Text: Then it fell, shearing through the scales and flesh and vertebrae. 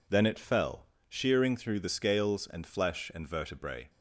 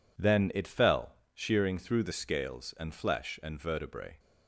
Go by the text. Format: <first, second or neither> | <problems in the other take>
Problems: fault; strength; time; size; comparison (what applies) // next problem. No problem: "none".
neither | none